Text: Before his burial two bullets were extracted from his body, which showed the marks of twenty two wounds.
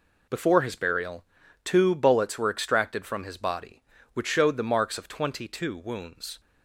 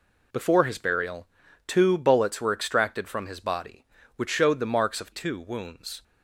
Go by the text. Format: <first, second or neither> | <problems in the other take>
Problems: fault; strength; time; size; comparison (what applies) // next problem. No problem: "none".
first | pauses between "burial" and "two"; at 1.2 s; 0.40 s long; also in the first // skips "twenty"; at 5.1 s